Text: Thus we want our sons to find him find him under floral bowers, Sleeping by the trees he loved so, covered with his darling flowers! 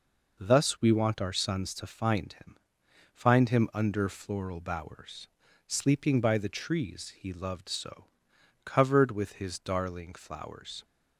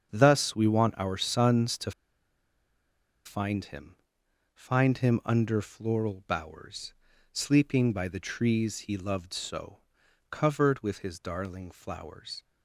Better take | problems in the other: first | starts louder than the rest; strong; until 1.1 s; 7 dB // pauses between "to" and "find"; strong; at 1.9 s; 1.3 s long // pauses between "him" and "find"; noticeable; at 3.9 s; 0.58 s long; noticeable in the first

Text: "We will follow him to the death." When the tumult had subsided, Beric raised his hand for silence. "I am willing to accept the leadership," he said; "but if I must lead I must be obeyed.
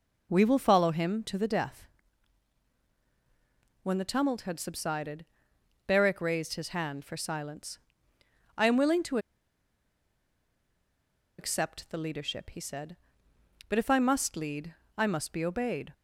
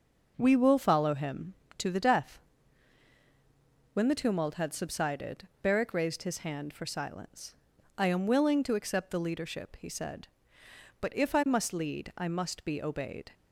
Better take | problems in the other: second | pauses between "to" and "accept"; strong; at 9.1 s; 2.2 s long // pauses between "lead" and "I"; slight; at 14.7 s; 0.22 s long

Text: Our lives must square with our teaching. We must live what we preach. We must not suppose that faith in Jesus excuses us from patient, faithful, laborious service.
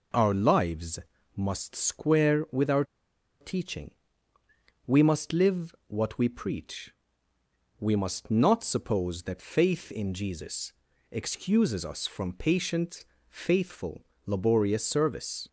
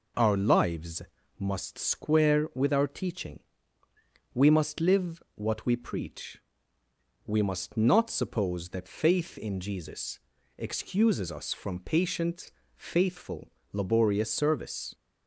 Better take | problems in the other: second | pauses between "lives" and "must"; slight; at 0.9 s; 0.36 s long; slight in the second // pauses between "our" and "teaching"; noticeable; at 2.8 s; 0.55 s long // pauses between "Jesus" and "excuses"; at 10.7 s; 0.38 s long; also in the second

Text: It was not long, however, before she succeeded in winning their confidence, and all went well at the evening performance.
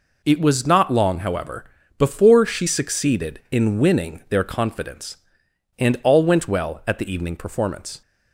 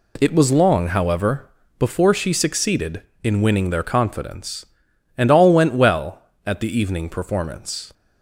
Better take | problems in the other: first | skips "not"; at 0.5 s

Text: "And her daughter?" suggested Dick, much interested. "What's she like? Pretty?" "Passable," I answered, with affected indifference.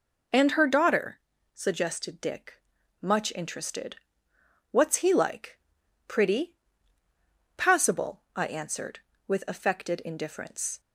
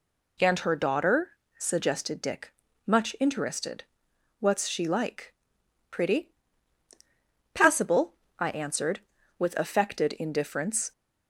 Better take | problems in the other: second | says "he" for "she"; at 4.9 s

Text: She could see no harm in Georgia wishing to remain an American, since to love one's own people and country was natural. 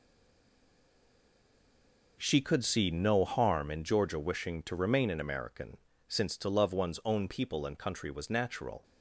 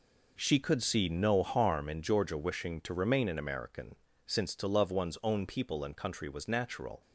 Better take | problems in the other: second | stays silent before the first word; until 2.1 s; 2.1 s long

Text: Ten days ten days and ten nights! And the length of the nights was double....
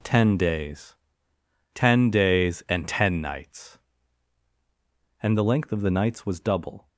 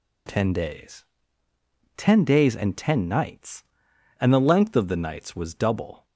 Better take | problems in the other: neither | pauses between "days" and "ten"; noticeable; the same in both

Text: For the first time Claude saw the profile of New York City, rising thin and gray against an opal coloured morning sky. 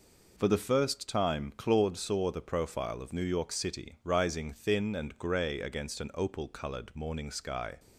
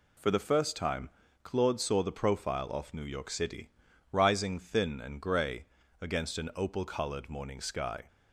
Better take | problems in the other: first | pauses between "time" and "Claude"; slight; at 1.0 s; 0.34 s long // says "off" for "of"; at 2.6 s // pauses between "gray" and "against"; slight; at 5.6 s; 0.34 s long

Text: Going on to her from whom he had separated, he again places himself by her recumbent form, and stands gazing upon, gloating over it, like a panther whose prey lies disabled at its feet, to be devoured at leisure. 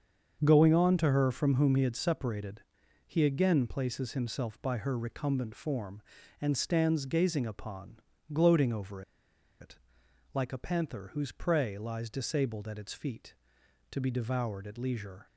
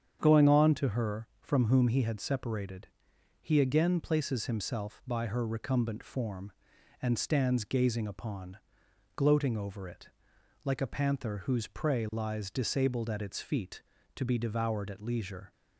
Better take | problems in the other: second | starts louder than the rest; until 1.4 s; 7 dB; strong in the second // pauses between "over" and "it"; noticeable; at 9.0 s; 0.59 s long

